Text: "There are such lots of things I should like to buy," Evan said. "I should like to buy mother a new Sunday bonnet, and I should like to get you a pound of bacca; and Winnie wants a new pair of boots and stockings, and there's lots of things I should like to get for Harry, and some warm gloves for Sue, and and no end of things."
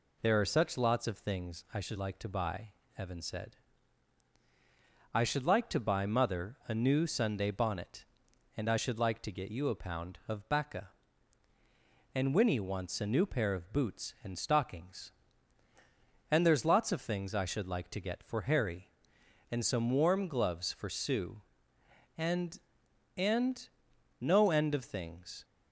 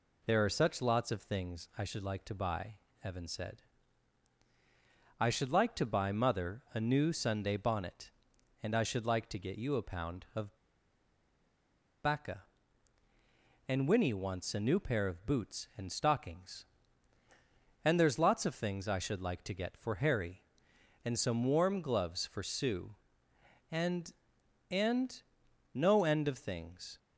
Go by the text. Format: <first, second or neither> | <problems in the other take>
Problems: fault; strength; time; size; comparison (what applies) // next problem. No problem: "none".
first | pauses between "of" and "bacca"; strong; at 10.5 s; 1.4 s long // pauses between "and" and "no"; noticeable; at 25.2 s; 0.52 s long; noticeable in the first